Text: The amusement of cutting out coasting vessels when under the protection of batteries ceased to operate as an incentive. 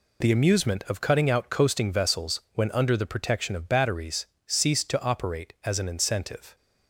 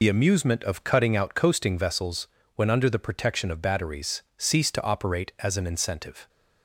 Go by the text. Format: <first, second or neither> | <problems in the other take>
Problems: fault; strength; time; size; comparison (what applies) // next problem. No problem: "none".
first | loses the start of "The"; at 0.0 s; 70 ms // pauses between "vessels" and "when"; slight; at 2.2 s; 0.28 s long // pauses between "batteries" and "ceased"; slight; at 4.2 s; 0.16 s long; slight in the first